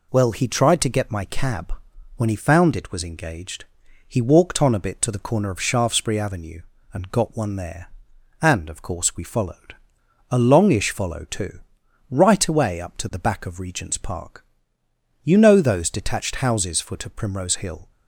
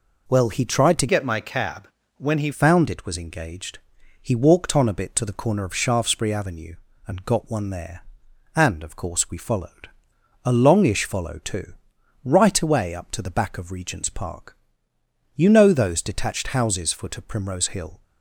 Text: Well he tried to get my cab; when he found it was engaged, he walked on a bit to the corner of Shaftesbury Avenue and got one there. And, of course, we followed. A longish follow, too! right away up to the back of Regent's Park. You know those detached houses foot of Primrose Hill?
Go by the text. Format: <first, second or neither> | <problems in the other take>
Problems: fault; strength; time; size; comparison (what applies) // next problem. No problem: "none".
first | changes voice from "get" to "he"; from 1.0 to 2.5 s; 1.5 s long